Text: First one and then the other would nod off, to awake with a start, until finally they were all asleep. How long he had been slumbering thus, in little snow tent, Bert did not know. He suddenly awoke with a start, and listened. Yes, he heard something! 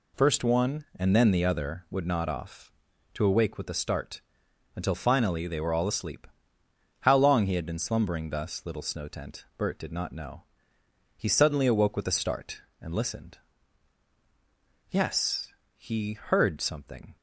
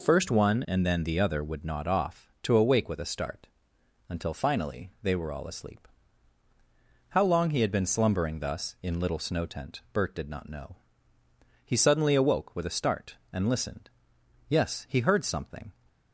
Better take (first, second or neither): second